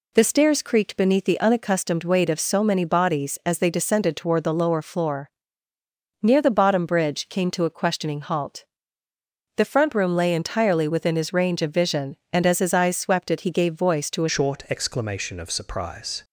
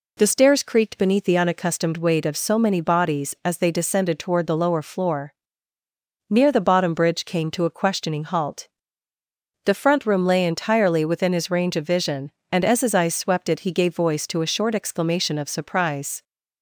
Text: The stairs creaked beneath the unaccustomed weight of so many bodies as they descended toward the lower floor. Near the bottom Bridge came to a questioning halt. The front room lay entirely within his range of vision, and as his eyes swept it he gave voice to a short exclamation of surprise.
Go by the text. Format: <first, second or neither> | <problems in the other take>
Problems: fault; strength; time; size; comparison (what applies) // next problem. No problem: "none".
second | changes voice at "short"; from 14.2 s on; 2.0 s long